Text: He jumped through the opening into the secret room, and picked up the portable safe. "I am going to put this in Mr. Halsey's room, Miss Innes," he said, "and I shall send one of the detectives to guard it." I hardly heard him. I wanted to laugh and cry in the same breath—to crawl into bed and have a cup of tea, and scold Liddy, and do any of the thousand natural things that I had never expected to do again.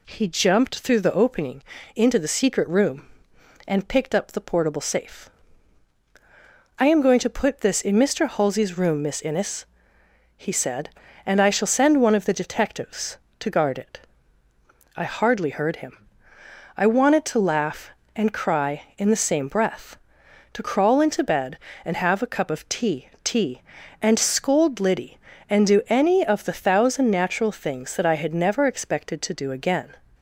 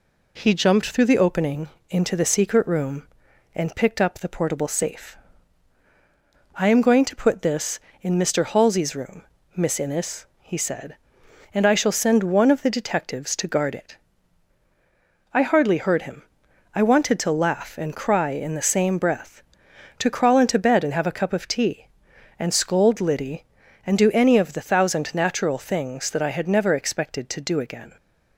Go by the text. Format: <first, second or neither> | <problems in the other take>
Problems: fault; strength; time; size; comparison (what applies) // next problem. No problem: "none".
second | pauses between "opening" and "into"; slight; at 1.6 s; 0.36 s long; slight in the second // says "tea" twice; at 23.2 s